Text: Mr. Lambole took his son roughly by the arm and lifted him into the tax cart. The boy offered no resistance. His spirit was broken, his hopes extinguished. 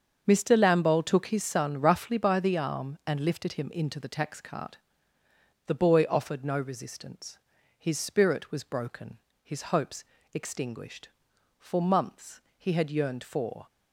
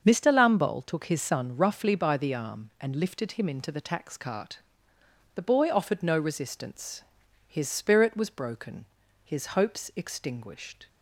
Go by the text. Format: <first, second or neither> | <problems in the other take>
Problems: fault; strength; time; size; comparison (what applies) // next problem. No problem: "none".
second | starts louder than the rest; until 1.2 s; 7 dB; also in the second // pauses between "hopes" and "extinguished"; slight; at 10.0 s; 0.30 s long // goes on to say "For months he had yearned for"; strong; from 11.5 s on; 2.0 s long